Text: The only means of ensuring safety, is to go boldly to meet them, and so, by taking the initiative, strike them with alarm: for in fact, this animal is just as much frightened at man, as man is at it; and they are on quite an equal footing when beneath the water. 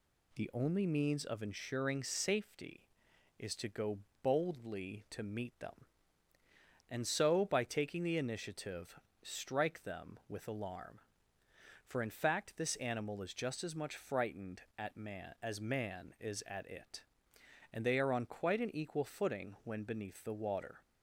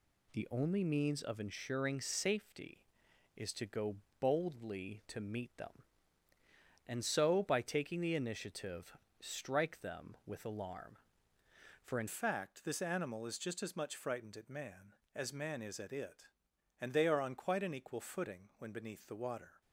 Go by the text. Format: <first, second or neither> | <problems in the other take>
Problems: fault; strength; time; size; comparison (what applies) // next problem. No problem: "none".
first | pauses between "go" and "boldly"; slight; at 3.9 s; 0.24 s long; slight in the first // changes voice at "fact"; from 12.0 s on; 7.6 s long